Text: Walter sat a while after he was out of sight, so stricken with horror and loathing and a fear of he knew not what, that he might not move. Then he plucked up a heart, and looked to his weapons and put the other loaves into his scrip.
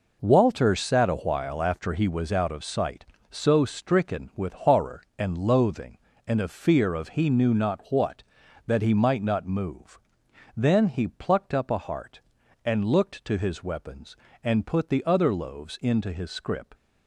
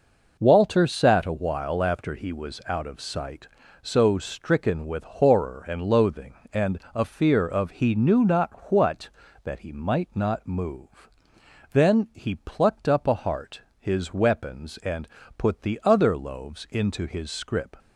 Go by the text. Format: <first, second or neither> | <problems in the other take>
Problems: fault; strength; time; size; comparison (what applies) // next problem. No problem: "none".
first | pauses between "and" and "a"; slight; at 6.7 s; 0.16 s long // pauses between "not" and "what"; slight; at 8.5 s; 0.18 s long // skips "and looked to"; at 13.7 s // pauses between "and" and "put"; slight; at 15.0 s; 0.30 s long